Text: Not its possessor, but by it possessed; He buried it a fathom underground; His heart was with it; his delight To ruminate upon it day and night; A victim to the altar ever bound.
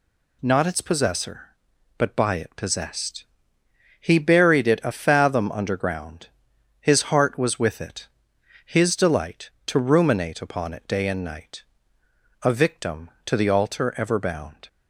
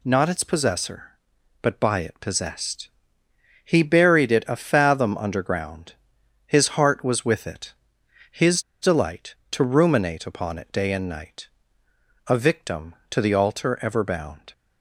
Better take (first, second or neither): first